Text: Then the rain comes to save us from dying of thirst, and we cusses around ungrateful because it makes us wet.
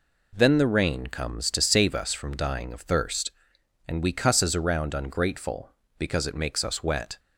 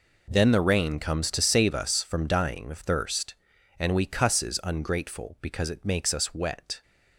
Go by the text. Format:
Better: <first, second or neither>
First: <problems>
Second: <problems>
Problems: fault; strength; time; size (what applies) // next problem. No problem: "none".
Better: first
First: none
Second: skips "around"; at 4.6 s